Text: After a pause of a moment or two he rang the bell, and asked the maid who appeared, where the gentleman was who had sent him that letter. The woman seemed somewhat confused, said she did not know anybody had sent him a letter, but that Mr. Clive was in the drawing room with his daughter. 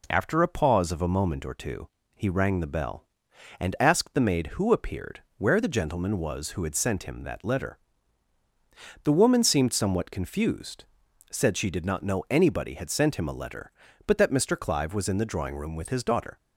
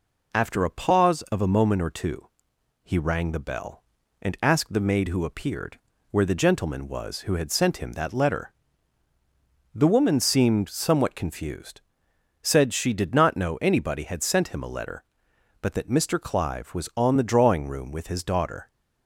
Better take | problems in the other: first | pauses between "two" and "he"; noticeable; at 2.2 s; 0.56 s long; slight in the first // says "on" for "in"; at 16.9 s

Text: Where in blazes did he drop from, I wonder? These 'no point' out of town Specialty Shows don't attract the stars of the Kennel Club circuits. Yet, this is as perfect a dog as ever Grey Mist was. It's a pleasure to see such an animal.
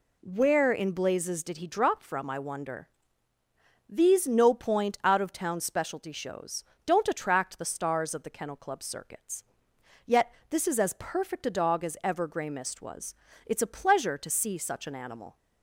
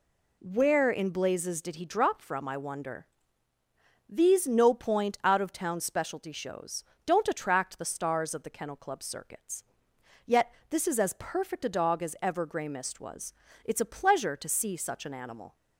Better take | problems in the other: neither | pauses between "Shows" and "don't"; slight; the same in both

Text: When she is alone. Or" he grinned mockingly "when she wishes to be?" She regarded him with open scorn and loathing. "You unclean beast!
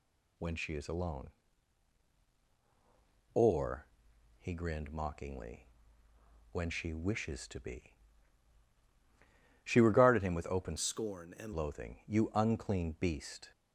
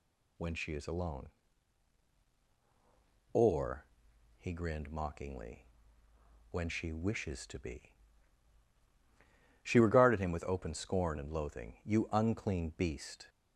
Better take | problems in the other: second | pauses between "Or" and "he"; noticeable; at 3.8 s; 0.54 s long; noticeable in the second // pauses between "mockingly" and "when"; noticeable; at 5.6 s; 0.84 s long; noticeable in the second // changes voice from "scorn" to "and"; from 10.7 to 11.5 s; 0.8 s long

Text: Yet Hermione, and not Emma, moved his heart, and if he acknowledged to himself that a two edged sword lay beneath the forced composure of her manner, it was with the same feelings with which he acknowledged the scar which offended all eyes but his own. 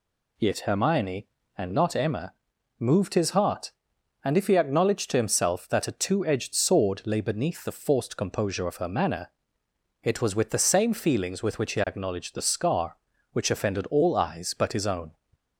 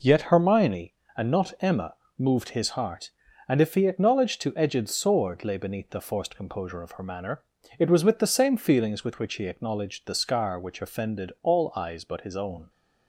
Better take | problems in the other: first | skips "himself that a two"; at 4.5 s

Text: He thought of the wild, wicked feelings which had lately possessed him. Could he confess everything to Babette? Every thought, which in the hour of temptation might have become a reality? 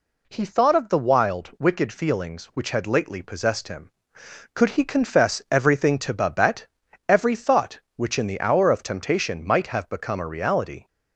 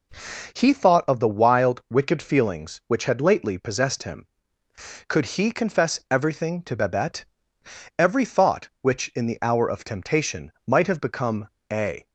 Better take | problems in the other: first | pauses between "become" and "a"; slight; at 11.4 s; 0.24 s long // stops before "reality"; at 12.0 s

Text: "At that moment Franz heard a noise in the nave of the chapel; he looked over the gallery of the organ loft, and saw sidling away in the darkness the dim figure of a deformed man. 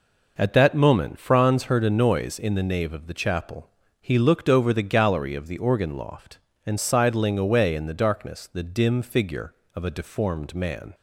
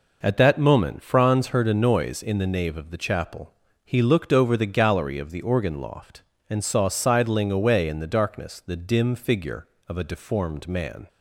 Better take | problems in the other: second | skips "saw"; at 6.7 s

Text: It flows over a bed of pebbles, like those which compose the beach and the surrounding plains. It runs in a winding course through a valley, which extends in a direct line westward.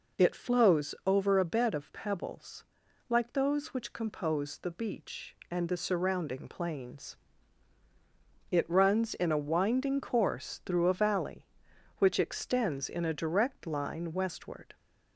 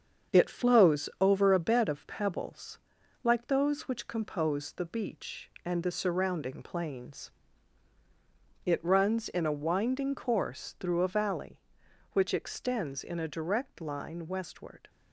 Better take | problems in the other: first | gets quieter; noticeable; throughout; 5.5 dB

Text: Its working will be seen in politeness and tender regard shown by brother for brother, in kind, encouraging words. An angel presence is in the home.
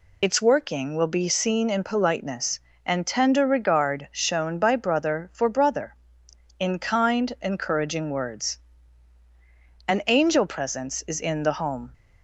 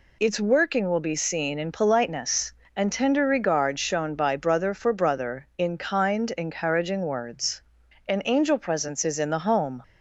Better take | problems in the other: second | loses the start of "Its"; at 0.2 s; 40 ms

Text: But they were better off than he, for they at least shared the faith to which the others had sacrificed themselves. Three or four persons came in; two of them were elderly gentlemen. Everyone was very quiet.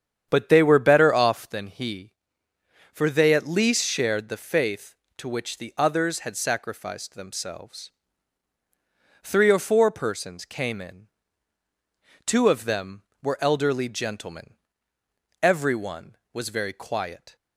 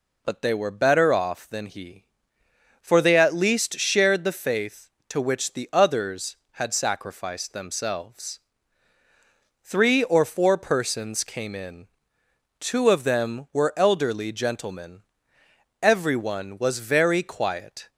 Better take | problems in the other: second | starts louder than the rest; strong; until 1.6 s; 8.5 dB

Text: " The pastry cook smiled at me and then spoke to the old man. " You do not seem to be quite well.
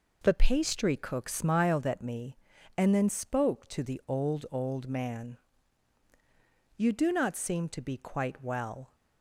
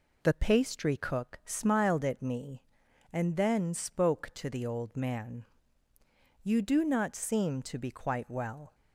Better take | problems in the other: second | says "old" twice; at 4.5 s

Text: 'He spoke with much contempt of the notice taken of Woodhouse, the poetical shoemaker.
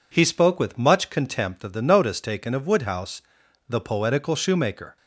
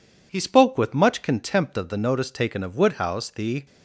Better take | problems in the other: first | stops before "poetical shoemaker"; at 3.6 s

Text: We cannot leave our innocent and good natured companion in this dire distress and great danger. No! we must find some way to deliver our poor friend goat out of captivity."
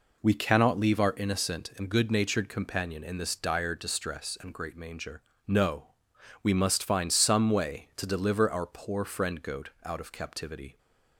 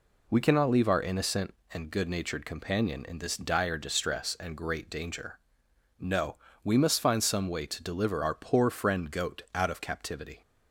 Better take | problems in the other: second | says "manger" for "danger"; at 4.7 s // pauses between "goat" and "out"; slight; at 9.6 s; 0.16 s long

